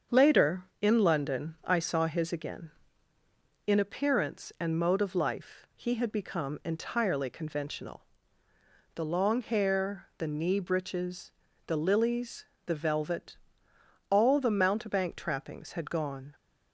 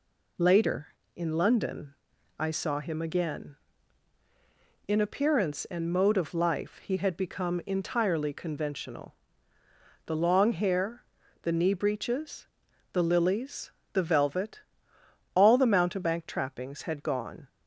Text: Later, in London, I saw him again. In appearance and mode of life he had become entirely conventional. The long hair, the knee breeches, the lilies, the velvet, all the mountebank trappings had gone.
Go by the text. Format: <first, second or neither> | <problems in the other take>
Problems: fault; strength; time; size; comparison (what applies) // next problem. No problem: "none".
second | starts louder than the rest; until 1.2 s; 7 dB // says "his" for "him"; at 2.0 s